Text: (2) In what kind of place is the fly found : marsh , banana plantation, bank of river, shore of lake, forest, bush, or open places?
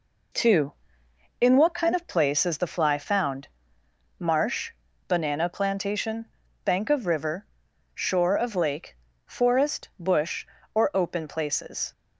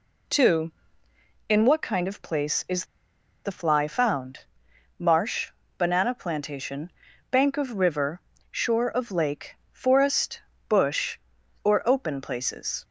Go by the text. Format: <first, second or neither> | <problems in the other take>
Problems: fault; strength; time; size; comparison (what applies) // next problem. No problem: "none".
first | pauses between "is" and "the"; noticeable; at 2.8 s; 0.58 s long